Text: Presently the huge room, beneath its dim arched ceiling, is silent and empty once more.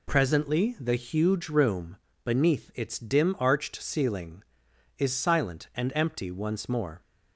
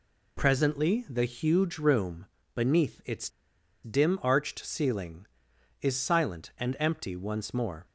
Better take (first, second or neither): first